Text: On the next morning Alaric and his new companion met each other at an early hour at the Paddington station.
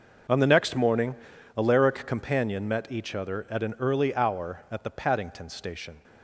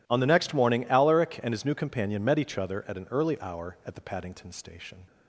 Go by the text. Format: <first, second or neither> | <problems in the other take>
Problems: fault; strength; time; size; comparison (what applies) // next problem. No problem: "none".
second | starts louder than the rest; noticeable; until 1.7 s; 6 dB // pauses between "morning" and "Alaric"; at 1.1 s; 0.42 s long // skips "and his new"; at 2.0 s